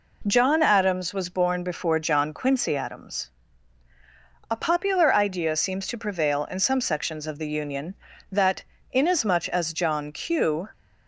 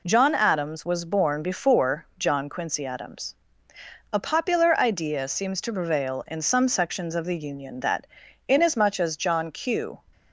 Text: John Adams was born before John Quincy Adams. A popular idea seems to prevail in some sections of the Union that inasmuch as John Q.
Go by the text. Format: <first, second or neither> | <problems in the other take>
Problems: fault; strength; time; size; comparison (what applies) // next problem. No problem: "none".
neither | pauses between "that" and "inasmuch"; the same in both